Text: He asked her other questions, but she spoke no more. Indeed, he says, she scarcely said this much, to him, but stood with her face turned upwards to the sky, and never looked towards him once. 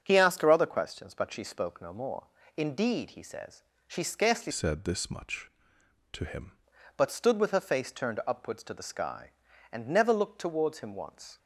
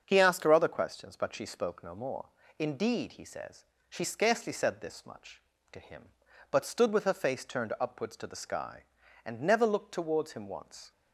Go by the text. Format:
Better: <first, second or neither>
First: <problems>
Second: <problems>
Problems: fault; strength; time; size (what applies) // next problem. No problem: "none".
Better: second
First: starts louder than the rest; until 1.0 s; 7 dB // changes voice from "said" to "him"; from 4.5 to 6.5 s; 2.0 s long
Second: starts louder than the rest; until 1.0 s; 7 dB